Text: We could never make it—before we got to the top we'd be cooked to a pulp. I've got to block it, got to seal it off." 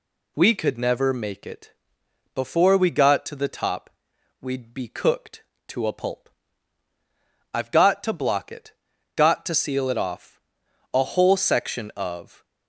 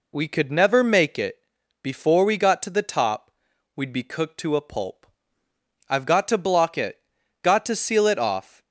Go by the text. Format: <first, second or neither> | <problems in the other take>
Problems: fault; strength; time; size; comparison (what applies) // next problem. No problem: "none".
second | pauses between "top" and "we'd"; noticeable; at 3.8 s; 0.50 s long; also in the second // goes on to say "A whole section of"; from 10.9 s on; 1.5 s long